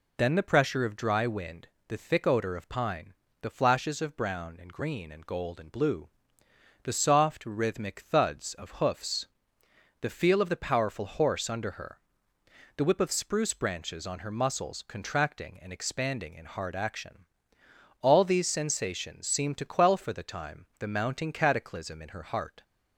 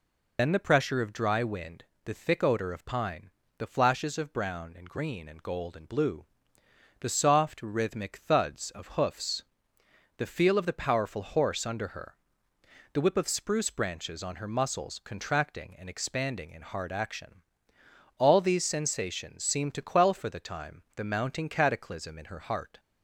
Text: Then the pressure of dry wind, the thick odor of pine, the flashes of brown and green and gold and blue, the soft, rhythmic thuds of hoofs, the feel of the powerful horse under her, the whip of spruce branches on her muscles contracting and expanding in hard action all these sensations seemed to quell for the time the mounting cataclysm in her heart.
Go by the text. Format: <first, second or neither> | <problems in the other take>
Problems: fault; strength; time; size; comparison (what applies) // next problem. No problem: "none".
first | loses the start of "Then"; at 0.3 s; 40 ms // pauses between "action" and "all"; noticeable; at 17.4 s; 0.76 s long; noticeable in the first